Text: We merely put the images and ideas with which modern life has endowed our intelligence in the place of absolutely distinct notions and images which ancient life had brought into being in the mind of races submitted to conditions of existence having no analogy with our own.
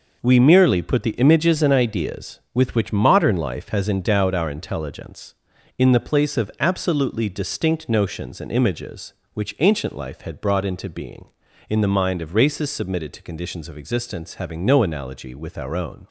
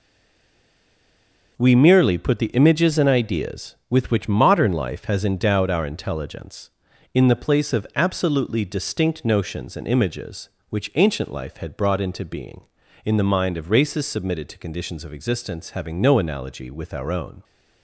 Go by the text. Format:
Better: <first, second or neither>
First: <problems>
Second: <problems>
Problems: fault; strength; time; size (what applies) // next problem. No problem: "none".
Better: first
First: none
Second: stays silent before the first word; noticeable; until 1.5 s; 1.5 s long